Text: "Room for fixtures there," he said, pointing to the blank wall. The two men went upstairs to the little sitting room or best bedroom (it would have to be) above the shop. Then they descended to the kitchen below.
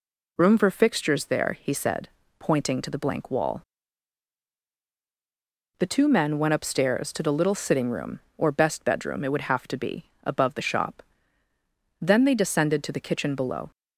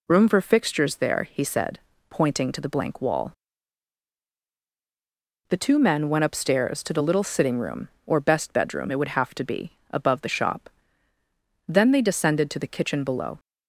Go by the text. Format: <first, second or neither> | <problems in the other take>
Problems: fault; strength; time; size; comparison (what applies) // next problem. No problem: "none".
neither | none